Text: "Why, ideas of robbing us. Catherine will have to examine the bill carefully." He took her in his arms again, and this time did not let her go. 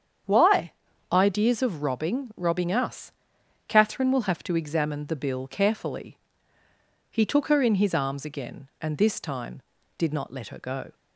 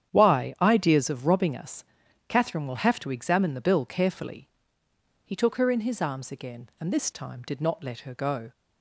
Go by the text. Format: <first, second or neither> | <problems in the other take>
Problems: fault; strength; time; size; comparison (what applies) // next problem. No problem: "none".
second | starts louder than the rest; strong; until 1.6 s; 8 dB; strong in the second // says "robbing" twice; at 2.3 s